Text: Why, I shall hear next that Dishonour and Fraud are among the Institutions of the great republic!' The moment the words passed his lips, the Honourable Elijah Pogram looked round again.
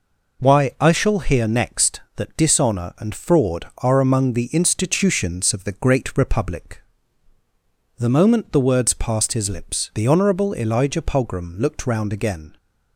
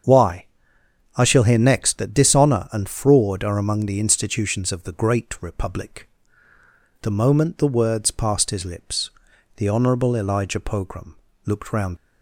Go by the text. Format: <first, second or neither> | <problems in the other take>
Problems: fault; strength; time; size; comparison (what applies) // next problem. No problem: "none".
first | starts louder than the rest; strong; until 1.7 s; 7.5 dB // pauses between "Pogram" and "looked"; slight; at 11.1 s; 0.30 s long // stops before "again"; at 11.9 s